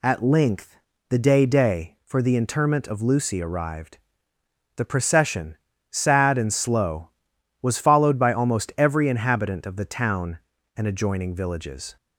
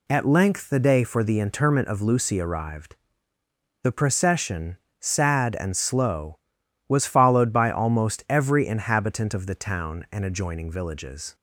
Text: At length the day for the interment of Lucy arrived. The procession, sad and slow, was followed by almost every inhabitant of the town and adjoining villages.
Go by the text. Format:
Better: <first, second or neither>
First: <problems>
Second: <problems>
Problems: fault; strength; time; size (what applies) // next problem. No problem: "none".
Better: second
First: pauses between "length" and "the"; slight; at 0.7 s; 0.32 s long // says "day" twice; at 1.4 s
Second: none